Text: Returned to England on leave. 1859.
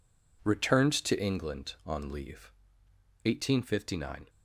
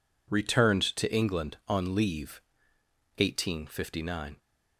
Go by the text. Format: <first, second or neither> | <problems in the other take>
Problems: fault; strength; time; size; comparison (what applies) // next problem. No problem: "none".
neither | none